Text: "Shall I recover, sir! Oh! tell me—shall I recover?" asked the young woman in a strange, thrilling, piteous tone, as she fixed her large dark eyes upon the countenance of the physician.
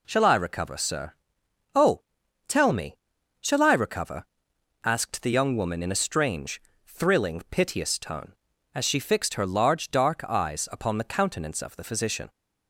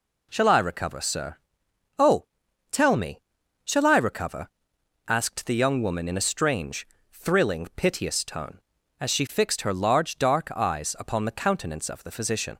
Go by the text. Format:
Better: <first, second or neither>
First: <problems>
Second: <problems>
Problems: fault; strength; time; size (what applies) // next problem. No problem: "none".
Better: neither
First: none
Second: none